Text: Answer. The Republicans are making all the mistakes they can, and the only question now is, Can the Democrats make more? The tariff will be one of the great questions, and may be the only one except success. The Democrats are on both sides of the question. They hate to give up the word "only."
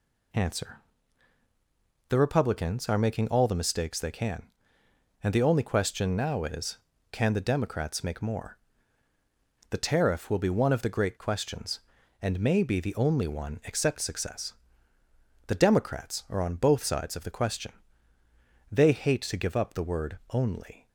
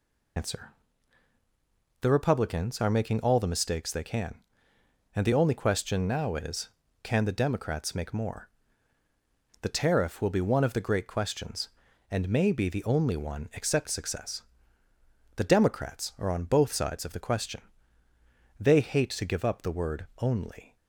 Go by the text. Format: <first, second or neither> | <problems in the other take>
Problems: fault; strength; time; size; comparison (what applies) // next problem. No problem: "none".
first | loses the start of "Answer"; at 0.3 s; 110 ms